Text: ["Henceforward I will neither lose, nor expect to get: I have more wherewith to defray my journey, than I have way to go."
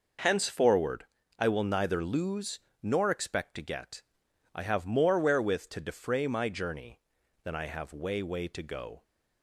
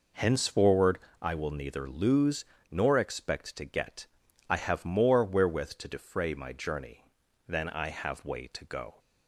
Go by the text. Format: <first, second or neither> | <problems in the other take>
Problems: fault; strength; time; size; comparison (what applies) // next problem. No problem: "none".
second | pauses between "Henceforward" and "I"; slight; at 1.0 s; 0.32 s long; slight in the second // says "way" twice; at 8.2 s